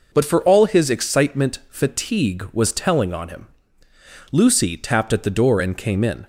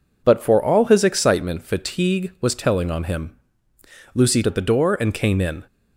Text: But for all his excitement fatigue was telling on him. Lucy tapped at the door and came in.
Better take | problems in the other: first | skips "tapped"; at 4.4 s

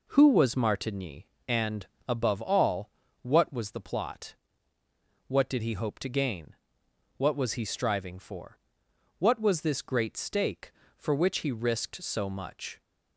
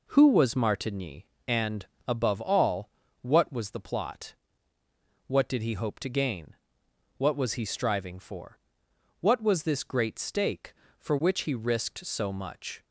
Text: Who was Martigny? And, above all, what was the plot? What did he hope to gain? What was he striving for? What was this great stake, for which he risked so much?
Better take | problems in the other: neither | none

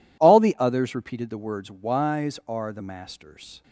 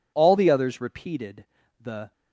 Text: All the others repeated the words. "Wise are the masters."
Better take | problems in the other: first | pauses between "repeated" and "the"; at 1.4 s; 0.38 s long // stops before "words Wise are the masters"; at 2.1 s

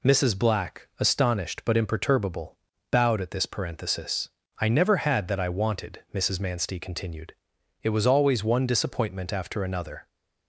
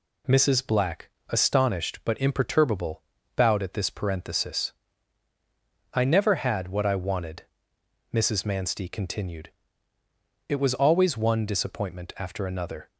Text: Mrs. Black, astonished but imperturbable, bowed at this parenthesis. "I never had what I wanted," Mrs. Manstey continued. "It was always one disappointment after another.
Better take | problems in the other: second | says "that" for "what"; at 5.2 s

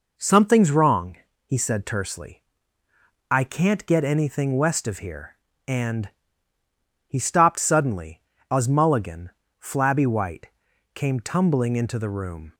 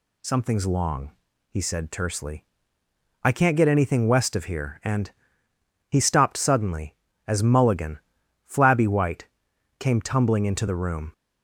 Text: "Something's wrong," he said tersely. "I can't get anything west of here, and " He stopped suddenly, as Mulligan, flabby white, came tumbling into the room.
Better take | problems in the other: first | says "long" for "wrong"; at 0.6 s

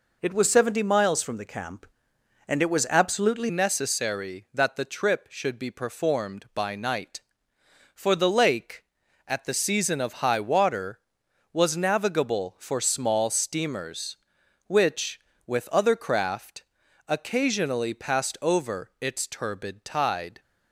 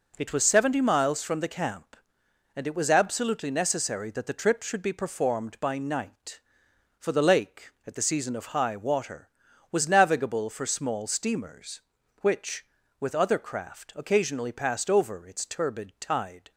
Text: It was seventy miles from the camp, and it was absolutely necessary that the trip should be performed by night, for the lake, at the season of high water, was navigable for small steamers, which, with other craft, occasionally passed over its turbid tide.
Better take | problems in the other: second | changes voice at "necessary"; from 3.5 s on; 16.9 s long

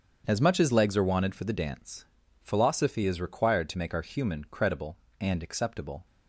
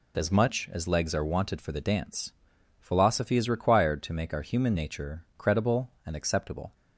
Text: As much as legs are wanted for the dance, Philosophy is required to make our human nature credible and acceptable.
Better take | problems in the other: second | starts louder than the rest; strong; until 1.2 s; 7.5 dB // skips "nature"; at 4.4 s

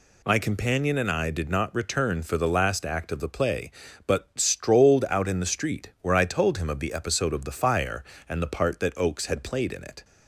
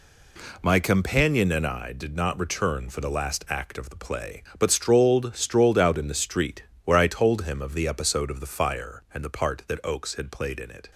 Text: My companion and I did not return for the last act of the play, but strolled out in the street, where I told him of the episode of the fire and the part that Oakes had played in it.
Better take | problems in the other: first | says "strolled" twice; at 5.3 s

